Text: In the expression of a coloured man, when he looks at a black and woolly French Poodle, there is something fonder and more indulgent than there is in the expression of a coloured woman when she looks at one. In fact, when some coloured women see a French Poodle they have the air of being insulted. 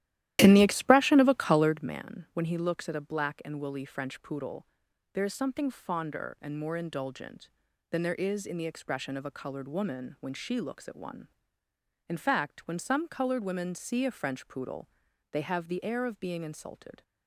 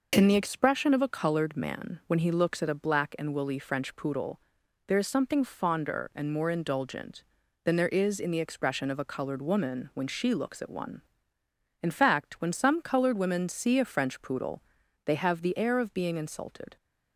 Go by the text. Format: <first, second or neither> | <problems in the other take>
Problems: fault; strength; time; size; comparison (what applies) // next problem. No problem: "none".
second | starts louder than the rest; strong; until 1.9 s; 13.5 dB // pauses between "Poodle" and "they"; at 14.8 s; 0.44 s long; also in the second